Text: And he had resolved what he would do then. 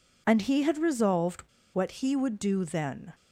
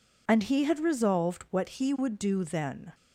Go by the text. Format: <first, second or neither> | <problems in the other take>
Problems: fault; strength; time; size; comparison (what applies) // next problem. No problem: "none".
second | pauses between "resolved" and "what"; slight; at 1.4 s; 0.32 s long